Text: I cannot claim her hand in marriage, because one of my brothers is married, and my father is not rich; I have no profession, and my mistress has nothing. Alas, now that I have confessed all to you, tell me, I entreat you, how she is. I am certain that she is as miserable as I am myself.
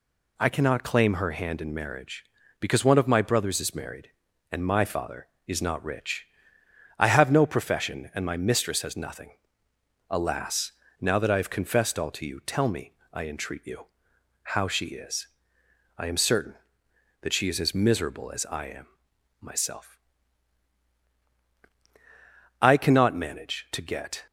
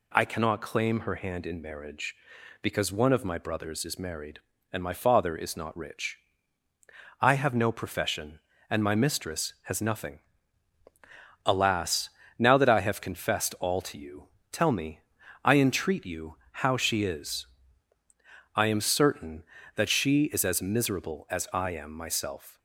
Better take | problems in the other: second | pauses between "am" and "myself"; noticeable; at 18.8 s; 0.52 s long // goes on to say "I cannot manage to get"; from 22.5 s on; 1.6 s long

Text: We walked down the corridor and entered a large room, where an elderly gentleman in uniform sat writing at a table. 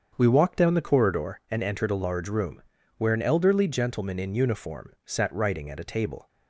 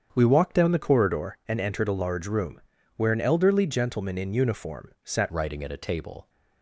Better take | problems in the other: first | starts louder than the rest; strong; until 1.1 s; 8 dB; strong in the first // changes voice at "writing"; from 5.3 s on; 0.9 s long

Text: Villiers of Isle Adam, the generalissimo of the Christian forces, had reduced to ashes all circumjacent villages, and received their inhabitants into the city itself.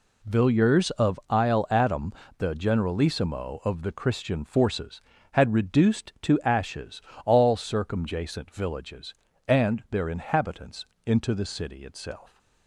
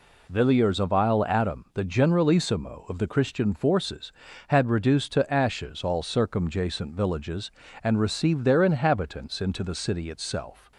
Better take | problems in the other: second | pauses between "ashes" and "all"; slight; at 7.0 s; 0.24 s long // skips "received"; at 9.8 s // pauses between "inhabitants" and "into"; slight; at 10.8 s; 0.20 s long

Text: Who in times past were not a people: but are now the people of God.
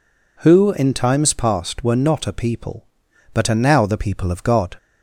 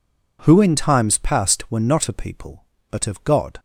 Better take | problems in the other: first | skips "are now the people"; at 3.0 s

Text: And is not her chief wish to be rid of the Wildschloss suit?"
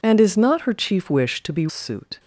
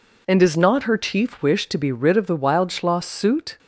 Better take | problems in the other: second | skips "rid of the Wildschloss"; at 1.6 s

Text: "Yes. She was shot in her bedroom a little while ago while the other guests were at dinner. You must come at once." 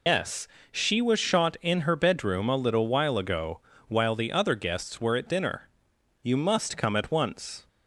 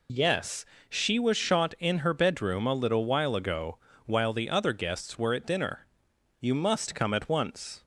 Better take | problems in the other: second | loses the start of "Yes"; at 0.0 s; 140 ms // pauses between "ago" and "while"; slight; at 3.5 s; 0.30 s long; slight in the second

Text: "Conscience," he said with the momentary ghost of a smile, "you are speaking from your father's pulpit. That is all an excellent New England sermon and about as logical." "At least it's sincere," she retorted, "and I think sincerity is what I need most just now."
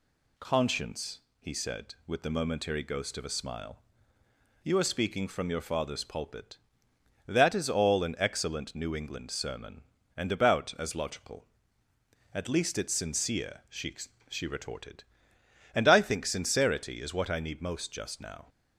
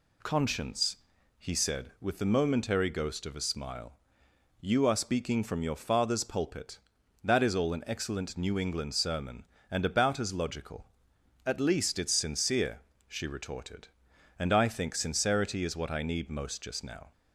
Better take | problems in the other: second | says "she" twice; at 14.2 s

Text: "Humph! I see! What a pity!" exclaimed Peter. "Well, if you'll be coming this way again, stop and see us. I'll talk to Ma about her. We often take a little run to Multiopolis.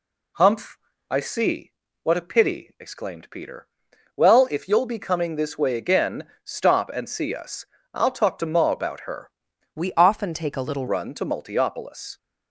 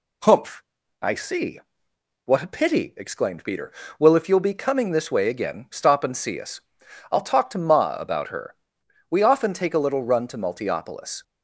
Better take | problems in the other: second | changes voice from "We" to "little"; from 9.7 to 10.8 s; 1.1 s long

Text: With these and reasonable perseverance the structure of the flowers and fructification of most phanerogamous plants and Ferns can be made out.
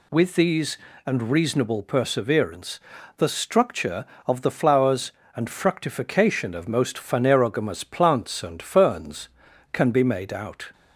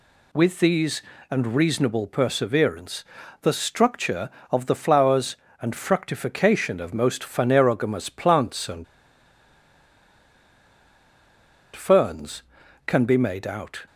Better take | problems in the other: first | pauses between "perseverance" and "the"; at 3.0 s; 0.38 s long; also in the first // pauses between "and" and "Ferns"; strong; at 8.8 s; 2.9 s long

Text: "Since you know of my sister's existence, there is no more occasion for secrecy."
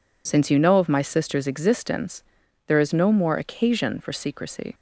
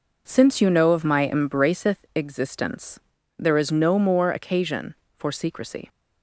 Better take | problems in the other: first | says "embraceth" for "sister's"; at 1.2 s

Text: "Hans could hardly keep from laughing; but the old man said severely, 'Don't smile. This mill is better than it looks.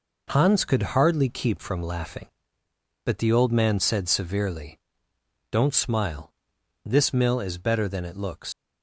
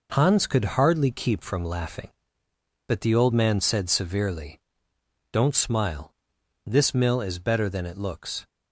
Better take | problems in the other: second | leaves "looks" unfinished; at 8.5 s; 140 ms

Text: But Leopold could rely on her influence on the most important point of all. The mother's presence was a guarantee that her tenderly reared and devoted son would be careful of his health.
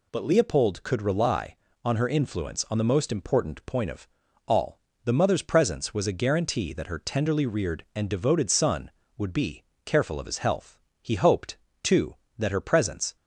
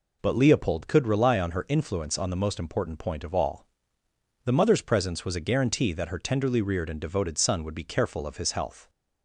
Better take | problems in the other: second | pauses between "of" and "all"; at 4.0 s; 0.40 s long // pauses between "be" and "careful"; slight; at 9.6 s; 0.22 s long // goes on to say "He hoped too that her presence"; strong; from 11.0 s on; 2.1 s long

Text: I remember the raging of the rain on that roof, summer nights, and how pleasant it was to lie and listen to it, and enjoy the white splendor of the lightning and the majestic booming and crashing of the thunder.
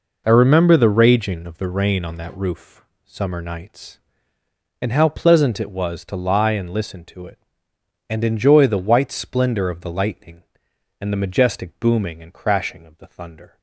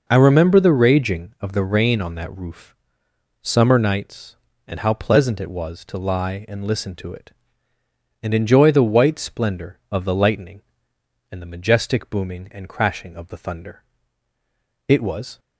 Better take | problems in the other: first | goes on to say "It was"; from 14.8 s on; 0.52 s long

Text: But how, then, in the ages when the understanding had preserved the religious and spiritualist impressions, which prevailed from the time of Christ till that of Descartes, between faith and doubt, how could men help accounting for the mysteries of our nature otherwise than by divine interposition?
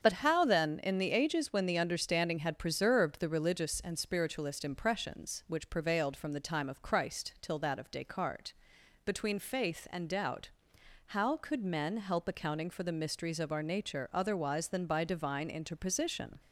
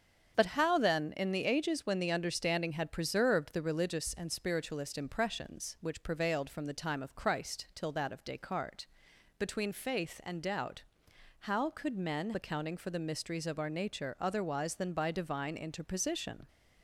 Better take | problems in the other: first | starts louder than the rest; strong; until 1.3 s; 7.5 dB; strong in the first // skips "help"; at 12.3 s

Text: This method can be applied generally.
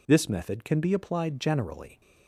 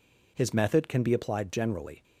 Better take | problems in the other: first | says "His" for "This"; at 0.3 s

